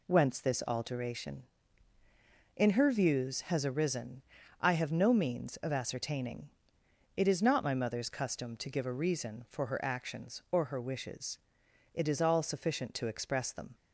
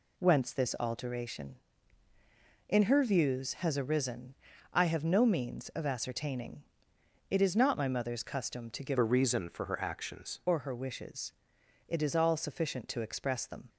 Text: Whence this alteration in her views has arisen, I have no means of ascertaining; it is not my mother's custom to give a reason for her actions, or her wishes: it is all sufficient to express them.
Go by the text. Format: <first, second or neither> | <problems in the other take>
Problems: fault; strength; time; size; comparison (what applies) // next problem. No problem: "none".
first | changes voice from "a" to "actions"; from 8.9 to 10.3 s; 1.4 s long